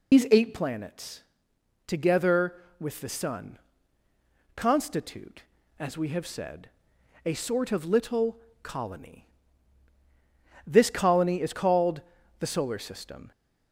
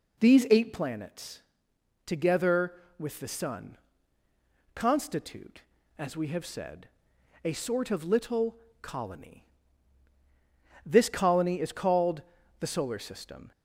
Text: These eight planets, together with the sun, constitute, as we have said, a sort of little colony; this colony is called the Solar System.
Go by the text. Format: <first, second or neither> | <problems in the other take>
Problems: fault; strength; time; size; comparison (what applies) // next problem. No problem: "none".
second | loses the start of "These"; at 0.1 s; 135 ms // pauses between "little" and "colony"; slight; at 8.3 s; 0.24 s long; slight in the second // pauses between "called" and "the"; at 12.0 s; 0.40 s long; also in the second